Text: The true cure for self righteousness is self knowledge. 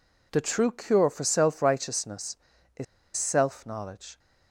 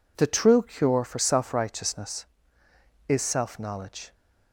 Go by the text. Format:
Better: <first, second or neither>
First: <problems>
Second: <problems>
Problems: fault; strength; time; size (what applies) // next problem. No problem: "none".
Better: second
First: pauses between "is" and "self"; slight; at 2.8 s; 0.31 s long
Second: none